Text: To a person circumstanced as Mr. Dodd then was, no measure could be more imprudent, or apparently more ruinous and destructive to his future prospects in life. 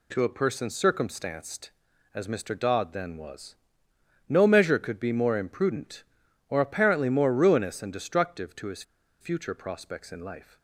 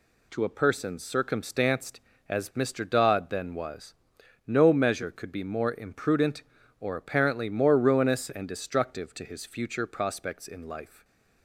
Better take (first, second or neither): second